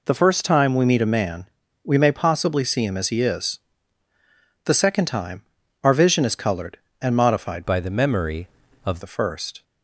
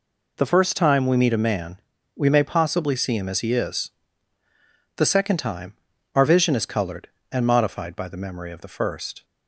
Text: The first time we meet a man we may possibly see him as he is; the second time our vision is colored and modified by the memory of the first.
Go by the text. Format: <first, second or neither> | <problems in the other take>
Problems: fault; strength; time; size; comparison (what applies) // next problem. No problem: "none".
second | pauses between "man" and "we"; at 1.4 s; 0.38 s long; also in the second // pauses between "time" and "our"; at 5.4 s; 0.38 s long; also in the second // changes voice from "by" to "of"; from 7.6 to 9.0 s; 1.4 s long